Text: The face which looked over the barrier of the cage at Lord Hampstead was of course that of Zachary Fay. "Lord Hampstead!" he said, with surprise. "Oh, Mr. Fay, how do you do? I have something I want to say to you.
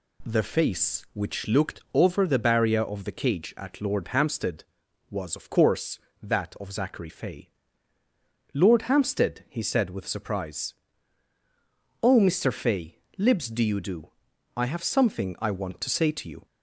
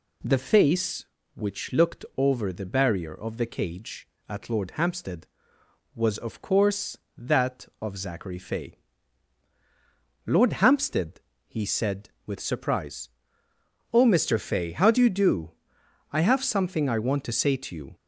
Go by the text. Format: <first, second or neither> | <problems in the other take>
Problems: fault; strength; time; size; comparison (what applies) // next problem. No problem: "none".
second | says "libs" for "how"; at 13.1 s